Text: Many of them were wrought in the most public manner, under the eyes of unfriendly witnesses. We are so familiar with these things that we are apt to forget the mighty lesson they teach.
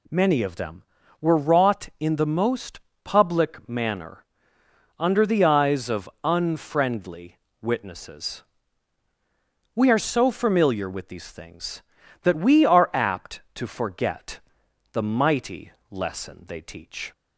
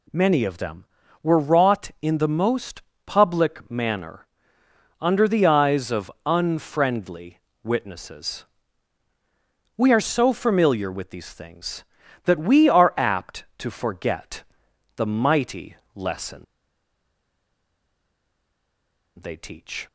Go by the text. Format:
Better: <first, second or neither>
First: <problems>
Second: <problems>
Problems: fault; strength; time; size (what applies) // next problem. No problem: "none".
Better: first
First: pauses between "most" and "public"; slight; at 2.8 s; 0.22 s long // pauses between "unfriendly" and "witnesses"; slight; at 7.3 s; 0.24 s long // pauses between "forget" and "the"; noticeable; at 14.3 s; 0.54 s long // pauses between "mighty" and "lesson"; slight; at 15.7 s; 0.18 s long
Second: pauses between "most" and "public"; slight; at 2.8 s; 0.22 s long // pauses between "unfriendly" and "witnesses"; slight; at 7.3 s; 0.24 s long // pauses between "forget" and "the"; noticeable; at 14.4 s; 0.54 s long // pauses between "mighty" and "lesson"; slight; at 15.7 s; 0.18 s long // pauses between "lesson" and "they"; strong; at 16.4 s; 2.7 s long